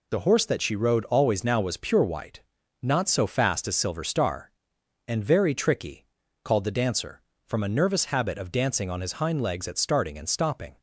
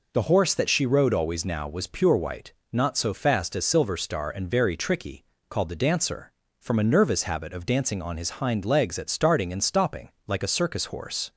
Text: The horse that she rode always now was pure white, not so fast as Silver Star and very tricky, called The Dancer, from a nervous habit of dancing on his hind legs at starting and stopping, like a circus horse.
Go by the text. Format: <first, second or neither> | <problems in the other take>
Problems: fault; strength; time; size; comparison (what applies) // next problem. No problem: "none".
second | stops before "like a circus horse"; at 10.7 s